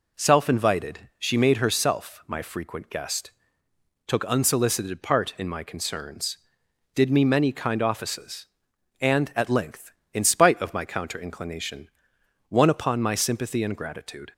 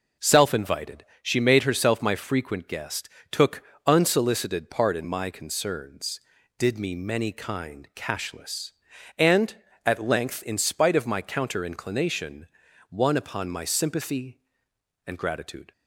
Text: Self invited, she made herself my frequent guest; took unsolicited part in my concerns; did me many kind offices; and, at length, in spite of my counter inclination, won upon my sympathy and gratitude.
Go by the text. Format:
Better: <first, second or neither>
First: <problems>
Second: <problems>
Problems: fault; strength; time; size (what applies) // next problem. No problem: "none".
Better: first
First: none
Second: pauses between "took" and "unsolicited"; slight; at 3.6 s; 0.24 s long // says "cashless" for "offices"; at 7.9 s